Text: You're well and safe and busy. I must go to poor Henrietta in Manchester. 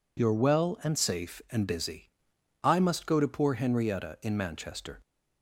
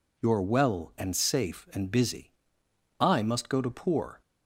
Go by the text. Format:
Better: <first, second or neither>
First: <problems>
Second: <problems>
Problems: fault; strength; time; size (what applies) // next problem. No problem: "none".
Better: first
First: none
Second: stops before "Henrietta in Manchester"; at 4.2 s